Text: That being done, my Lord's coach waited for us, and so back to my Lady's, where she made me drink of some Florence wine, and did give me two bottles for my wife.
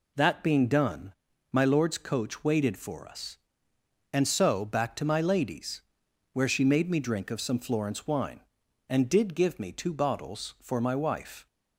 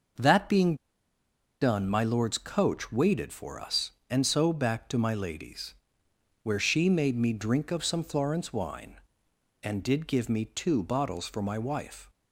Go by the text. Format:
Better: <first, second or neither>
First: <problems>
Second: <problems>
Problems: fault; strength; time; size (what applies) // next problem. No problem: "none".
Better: first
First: none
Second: starts louder than the rest; noticeable; until 2.0 s; 6 dB // pauses between "being" and "done"; noticeable; at 0.7 s; 0.85 s long